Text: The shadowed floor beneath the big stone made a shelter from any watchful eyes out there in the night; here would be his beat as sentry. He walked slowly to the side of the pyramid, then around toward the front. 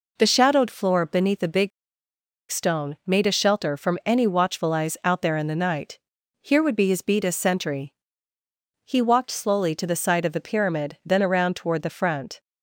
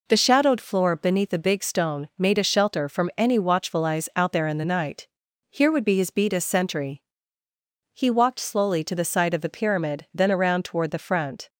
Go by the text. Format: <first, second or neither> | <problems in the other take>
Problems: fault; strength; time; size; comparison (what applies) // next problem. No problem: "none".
second | pauses between "big" and "stone"; noticeable; at 1.7 s; 0.81 s long